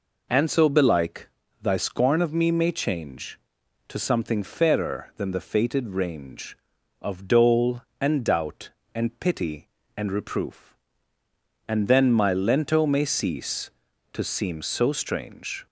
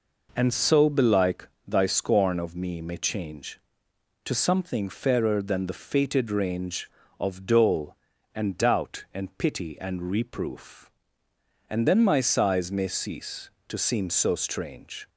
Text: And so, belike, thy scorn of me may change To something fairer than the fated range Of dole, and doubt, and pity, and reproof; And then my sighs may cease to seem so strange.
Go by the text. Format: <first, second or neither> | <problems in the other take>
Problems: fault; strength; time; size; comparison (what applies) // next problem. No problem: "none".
second | says "lento" for "sighs"; at 12.3 s